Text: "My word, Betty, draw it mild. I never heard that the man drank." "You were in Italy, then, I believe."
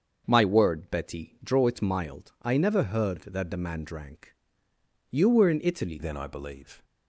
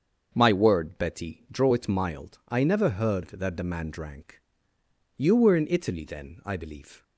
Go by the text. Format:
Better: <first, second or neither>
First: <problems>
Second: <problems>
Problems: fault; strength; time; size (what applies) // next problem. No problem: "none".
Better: second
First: starts louder than the rest; until 1.2 s; 6.5 dB // changes voice at "then"; from 5.9 s on; 0.9 s long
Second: starts louder than the rest; until 1.3 s; 6.5 dB